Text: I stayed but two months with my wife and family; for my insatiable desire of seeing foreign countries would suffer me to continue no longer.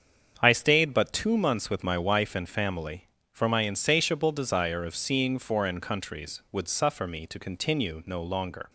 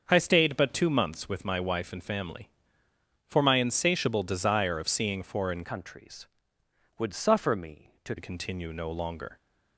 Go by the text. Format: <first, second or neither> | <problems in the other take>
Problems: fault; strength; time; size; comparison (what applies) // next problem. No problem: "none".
first | starts louder than the rest; until 1.1 s; 6.5 dB; strong in the first // changes voice from "countries" to "to"; from 5.6 to 8.1 s; 2.5 s long